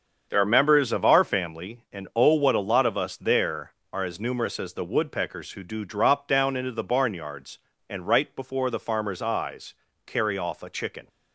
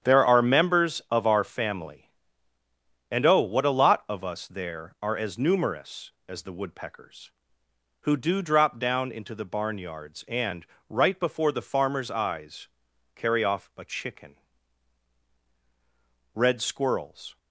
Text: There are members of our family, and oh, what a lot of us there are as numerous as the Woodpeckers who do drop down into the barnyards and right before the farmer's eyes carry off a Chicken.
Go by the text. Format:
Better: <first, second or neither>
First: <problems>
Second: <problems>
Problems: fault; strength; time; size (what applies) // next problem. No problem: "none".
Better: first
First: starts louder than the rest; until 1.3 s; 7 dB // pauses between "eyes" and "carry"; slight; at 9.7 s; 0.32 s long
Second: starts louder than the rest; strong; until 1.1 s; 9 dB // pauses between "and" and "right"; slight; at 10.6 s; 0.24 s long // pauses between "eyes" and "carry"; noticeable; at 12.6 s; 0.48 s long // goes on to say "Red Squirrels"; noticeable; from 16.3 s on; 1.0 s long